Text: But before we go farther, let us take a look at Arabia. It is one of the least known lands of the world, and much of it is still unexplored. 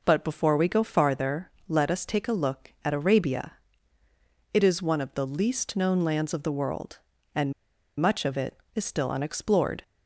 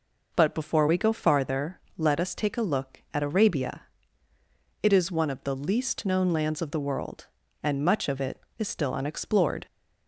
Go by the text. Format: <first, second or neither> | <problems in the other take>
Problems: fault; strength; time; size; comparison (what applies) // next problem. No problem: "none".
second | pauses between "and" and "much"; noticeable; at 7.5 s; 0.47 s long